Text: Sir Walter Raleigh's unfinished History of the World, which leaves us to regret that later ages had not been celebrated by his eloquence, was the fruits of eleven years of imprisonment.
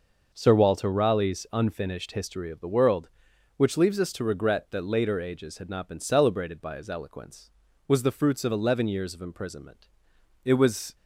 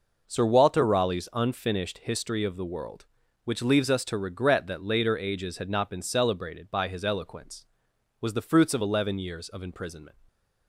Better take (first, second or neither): second